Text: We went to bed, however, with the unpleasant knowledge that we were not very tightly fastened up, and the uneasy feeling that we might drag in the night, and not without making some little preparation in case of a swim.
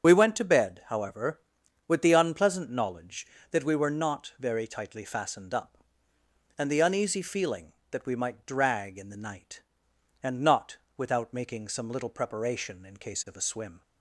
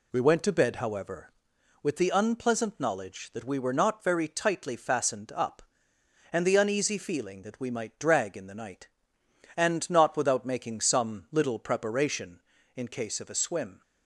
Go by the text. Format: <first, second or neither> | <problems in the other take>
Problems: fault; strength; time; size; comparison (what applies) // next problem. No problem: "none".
second | loses the start of "We"; at 0.0 s; 35 ms // starts louder than the rest; until 1.1 s; 6.5 dB // pauses between "not" and "without"; slight; at 10.7 s; 0.18 s long